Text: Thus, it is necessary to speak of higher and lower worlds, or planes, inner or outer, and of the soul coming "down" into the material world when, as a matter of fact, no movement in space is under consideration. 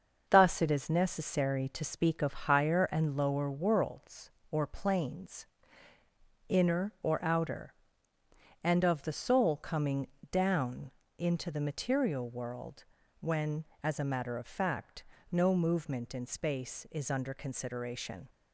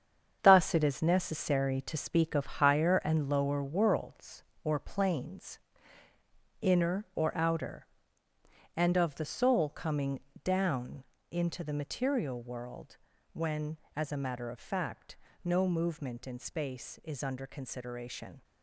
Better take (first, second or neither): first